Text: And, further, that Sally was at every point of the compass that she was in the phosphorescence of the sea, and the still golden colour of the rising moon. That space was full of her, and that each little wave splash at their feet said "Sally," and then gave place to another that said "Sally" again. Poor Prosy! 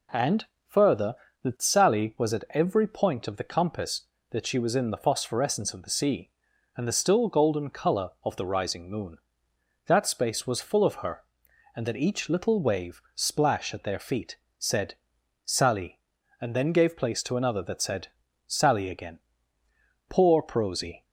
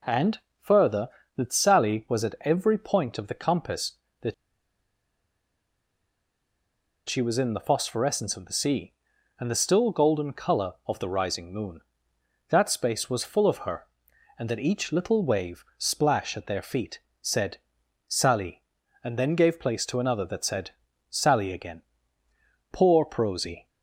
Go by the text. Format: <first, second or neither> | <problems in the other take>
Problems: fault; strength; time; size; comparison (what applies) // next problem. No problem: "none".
first | pauses between "that" and "she"; strong; at 4.3 s; 2.7 s long // pauses between "feet" and "said"; slight; at 16.9 s; 0.22 s long; slight in the first // pauses between "said" and "Sally"; noticeable; at 17.5 s; 0.50 s long; noticeable in the first // pauses between "said" and "Sally"; at 20.7 s; 0.38 s long; also in the first